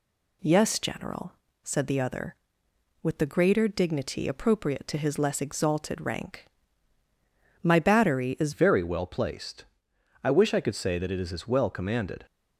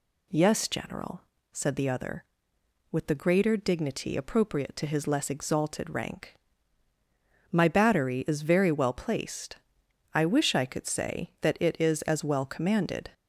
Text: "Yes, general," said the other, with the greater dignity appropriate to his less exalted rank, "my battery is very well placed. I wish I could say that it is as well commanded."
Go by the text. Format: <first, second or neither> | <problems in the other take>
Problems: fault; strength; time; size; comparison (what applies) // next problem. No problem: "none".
second | changes voice at "very"; from 8.5 s on; 3.7 s long